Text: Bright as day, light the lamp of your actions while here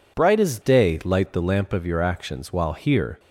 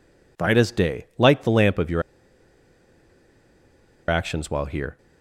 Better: first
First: none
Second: pauses between "your" and "actions"; strong; at 2.0 s; 2.0 s long

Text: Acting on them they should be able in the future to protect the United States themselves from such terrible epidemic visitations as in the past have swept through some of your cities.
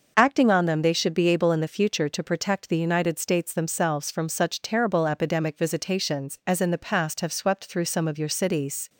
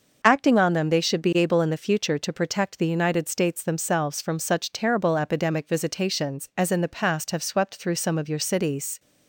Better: neither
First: starts louder than the rest; noticeable; until 1.1 s; 6 dB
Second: starts louder than the rest; noticeable; until 1.2 s; 6 dB

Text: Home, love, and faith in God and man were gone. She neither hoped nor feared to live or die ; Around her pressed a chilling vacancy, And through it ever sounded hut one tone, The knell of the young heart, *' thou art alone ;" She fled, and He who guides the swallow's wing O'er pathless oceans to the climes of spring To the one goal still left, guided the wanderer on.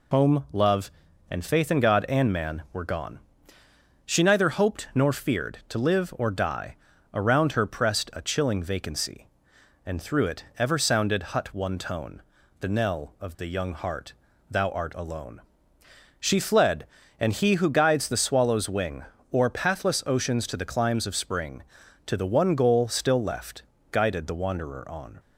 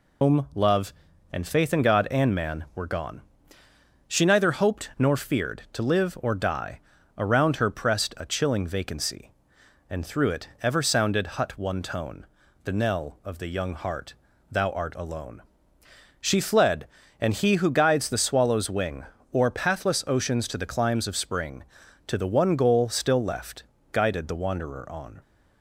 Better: first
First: pauses between "wing" and "O'er"; slight; at 19.0 s; 0.30 s long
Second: loses the start of "Home"; at 0.2 s; 75 ms // pauses between "wing" and "O'er"; slight; at 19.0 s; 0.30 s long

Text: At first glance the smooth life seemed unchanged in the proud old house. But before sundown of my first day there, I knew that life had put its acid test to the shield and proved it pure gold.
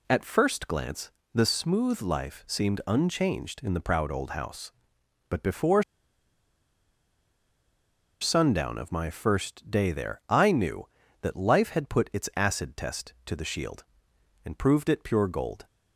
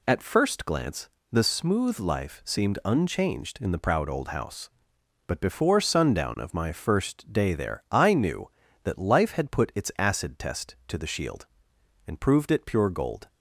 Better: second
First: pauses between "glance" and "the"; slight; at 1.1 s; 0.22 s long // pauses between "before" and "sundown"; strong; at 5.8 s; 2.3 s long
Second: pauses between "glance" and "the"; slight; at 1.0 s; 0.22 s long

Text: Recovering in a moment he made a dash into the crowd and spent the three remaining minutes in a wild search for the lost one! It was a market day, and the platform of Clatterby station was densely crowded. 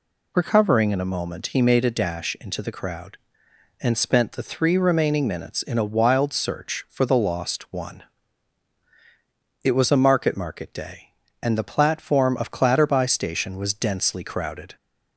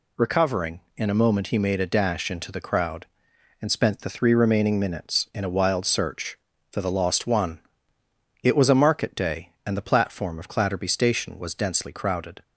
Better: second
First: says "market" twice; at 10.3 s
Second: none

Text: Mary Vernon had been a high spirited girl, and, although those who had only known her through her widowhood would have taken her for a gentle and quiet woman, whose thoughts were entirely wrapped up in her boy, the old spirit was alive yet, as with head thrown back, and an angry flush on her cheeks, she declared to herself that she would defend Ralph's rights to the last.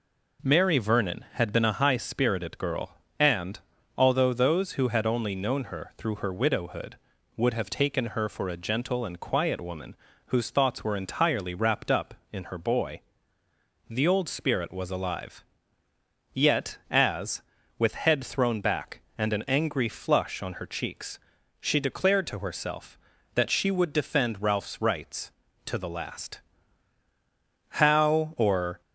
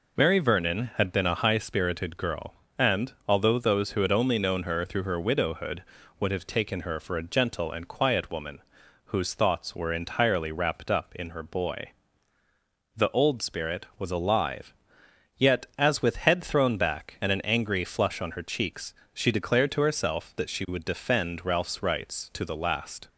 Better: second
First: pauses between "alive" and "yet"; noticeable; at 15.4 s; 0.90 s long // goes on to say "How or"; noticeable; from 27.6 s on; 1.1 s long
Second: pauses between "alive" and "yet"; noticeable; at 14.7 s; 0.64 s long

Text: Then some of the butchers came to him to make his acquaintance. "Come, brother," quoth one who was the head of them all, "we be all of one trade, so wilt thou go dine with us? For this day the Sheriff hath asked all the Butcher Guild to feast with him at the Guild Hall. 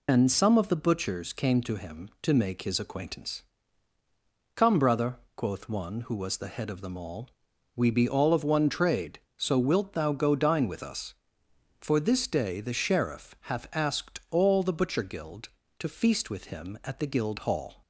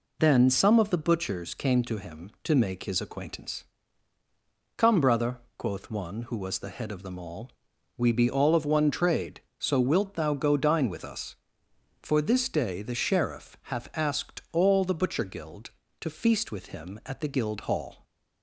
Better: second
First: loses the start of "Then"; at 0.0 s; 110 ms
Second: none

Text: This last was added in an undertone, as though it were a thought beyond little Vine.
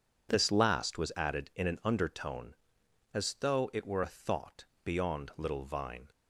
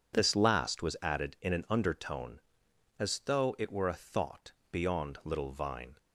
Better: neither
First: pauses between "thought" and "beyond"; slight; at 4.6 s; 0.18 s long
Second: pauses between "thought" and "beyond"; slight; at 4.5 s; 0.18 s long

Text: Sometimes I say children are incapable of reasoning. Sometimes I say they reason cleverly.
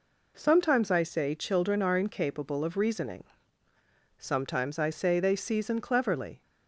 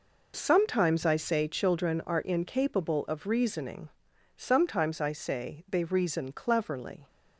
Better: second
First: says "season" for "reason"; at 5.3 s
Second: none

